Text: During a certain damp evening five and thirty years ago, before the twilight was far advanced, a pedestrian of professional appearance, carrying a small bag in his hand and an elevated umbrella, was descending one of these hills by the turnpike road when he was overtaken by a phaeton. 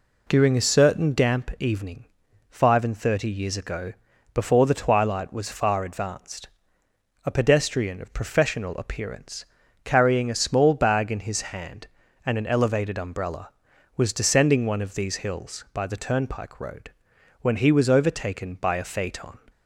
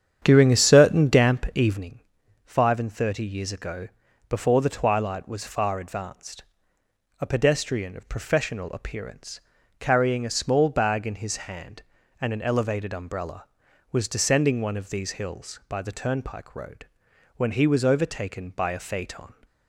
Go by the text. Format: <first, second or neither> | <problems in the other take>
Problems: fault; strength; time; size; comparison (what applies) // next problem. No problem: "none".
first | starts louder than the rest; strong; until 1.9 s; 9 dB // pauses between "evening" and "five"; noticeable; at 1.9 s; 0.46 s long; noticeable in the first // pauses between "road" and "when"; noticeable; at 16.8 s; 0.50 s long; noticeable in the first